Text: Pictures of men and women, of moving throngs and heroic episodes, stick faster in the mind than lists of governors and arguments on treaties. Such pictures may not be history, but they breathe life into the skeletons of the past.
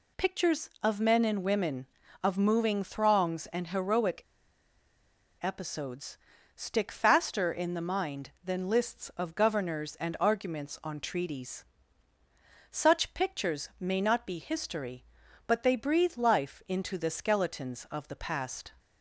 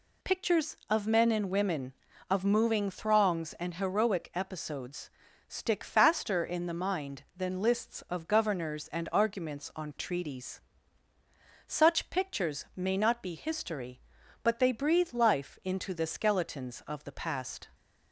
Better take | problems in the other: second | pauses between "heroic" and "episodes"; at 4.2 s; 1.1 s long

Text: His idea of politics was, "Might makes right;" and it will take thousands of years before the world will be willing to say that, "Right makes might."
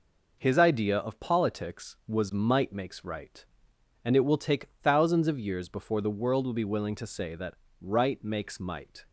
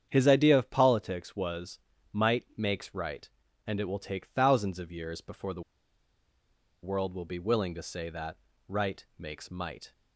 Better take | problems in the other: first | starts louder than the rest; strong; until 1.0 s; 8.5 dB // pauses between "the" and "world"; at 5.6 s; 1.2 s long

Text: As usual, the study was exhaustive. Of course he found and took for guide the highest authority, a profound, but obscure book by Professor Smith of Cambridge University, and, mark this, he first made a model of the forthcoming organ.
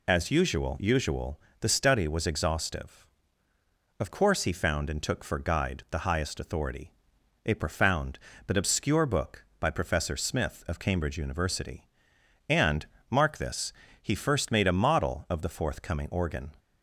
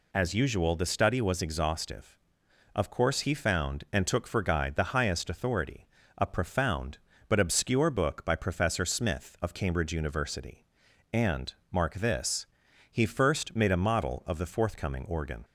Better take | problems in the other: second | says "usual" twice; at 0.7 s

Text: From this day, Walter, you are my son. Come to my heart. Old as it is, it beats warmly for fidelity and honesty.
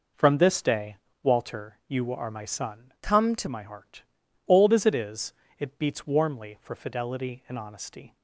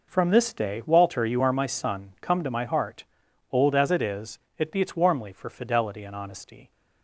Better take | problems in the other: second | changes voice from "Come" to "to"; from 3.0 to 3.4 s; 0.4 s long

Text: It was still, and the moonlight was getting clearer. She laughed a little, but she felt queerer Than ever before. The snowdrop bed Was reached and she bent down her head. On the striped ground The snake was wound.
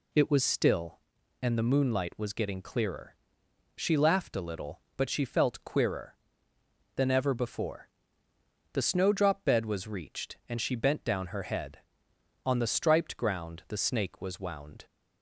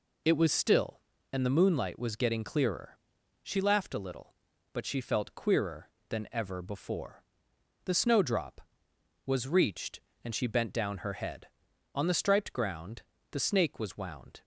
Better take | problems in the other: first | skips "bed"; at 8.9 s // pauses between "ground" and "The"; slight; at 13.0 s; 0.30 s long

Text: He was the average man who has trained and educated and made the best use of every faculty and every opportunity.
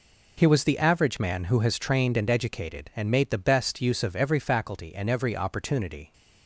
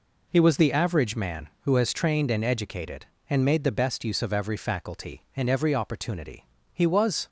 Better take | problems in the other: first | goes on to say "He was"; from 6.7 s on; 0.54 s long

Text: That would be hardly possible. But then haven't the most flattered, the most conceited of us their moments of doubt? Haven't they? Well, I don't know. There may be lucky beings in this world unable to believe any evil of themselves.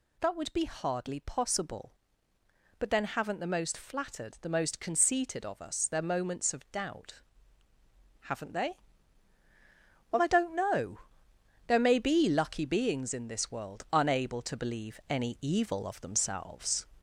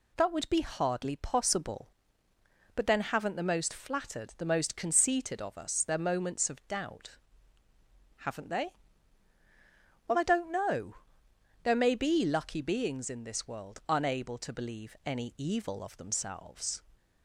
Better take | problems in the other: second | gets louder; slight; throughout; 3 dB

